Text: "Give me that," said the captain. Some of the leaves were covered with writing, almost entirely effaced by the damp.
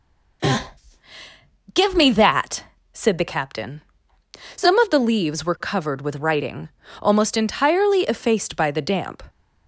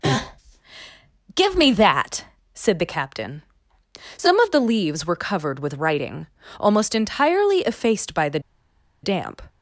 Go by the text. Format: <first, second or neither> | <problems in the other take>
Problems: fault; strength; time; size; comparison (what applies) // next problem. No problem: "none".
first | pauses between "the" and "damp"; noticeable; at 8.3 s; 0.64 s long